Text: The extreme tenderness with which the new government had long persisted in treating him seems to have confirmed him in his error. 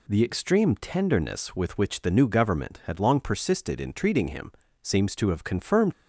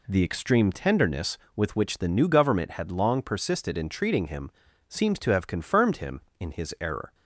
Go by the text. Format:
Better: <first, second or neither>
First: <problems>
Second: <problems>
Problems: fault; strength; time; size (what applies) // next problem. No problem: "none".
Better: second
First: pauses between "him" and "seems"; slight; at 4.5 s; 0.30 s long // stops before "him in his error"; at 5.9 s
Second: pauses between "him" and "seems"; slight; at 4.5 s; 0.36 s long